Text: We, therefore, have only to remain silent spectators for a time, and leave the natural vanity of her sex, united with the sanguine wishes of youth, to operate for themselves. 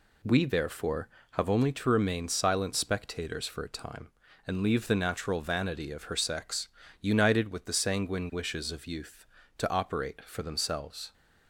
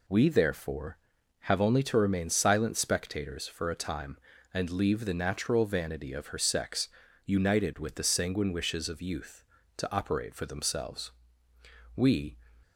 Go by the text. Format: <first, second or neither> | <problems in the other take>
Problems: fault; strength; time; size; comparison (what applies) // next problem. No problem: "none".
first | goes on to say "We"; slight; from 11.9 s on; 0.42 s long